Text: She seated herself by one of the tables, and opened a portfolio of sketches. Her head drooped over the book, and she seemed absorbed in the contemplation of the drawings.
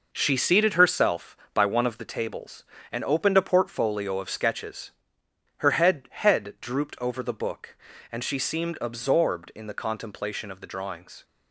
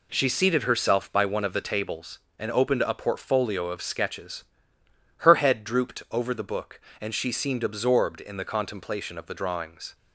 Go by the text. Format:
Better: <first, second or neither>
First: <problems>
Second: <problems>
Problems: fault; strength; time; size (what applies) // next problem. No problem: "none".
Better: second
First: says "head" twice; at 6.1 s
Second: none